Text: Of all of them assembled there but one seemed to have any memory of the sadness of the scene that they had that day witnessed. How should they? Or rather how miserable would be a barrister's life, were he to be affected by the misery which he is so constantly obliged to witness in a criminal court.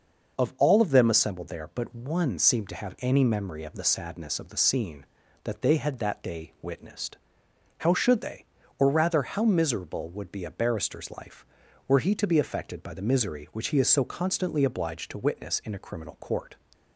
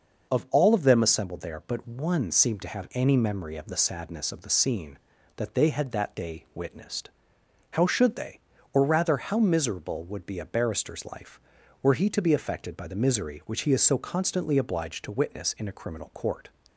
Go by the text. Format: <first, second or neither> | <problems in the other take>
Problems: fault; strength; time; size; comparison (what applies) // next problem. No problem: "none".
neither | none